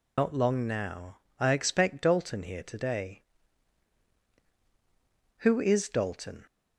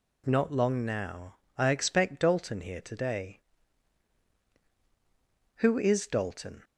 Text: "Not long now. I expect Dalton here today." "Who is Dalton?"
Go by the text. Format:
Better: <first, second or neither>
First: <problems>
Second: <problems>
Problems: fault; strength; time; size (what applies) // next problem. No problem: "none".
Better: second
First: loses the start of "Not"; at 0.1 s; 120 ms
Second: none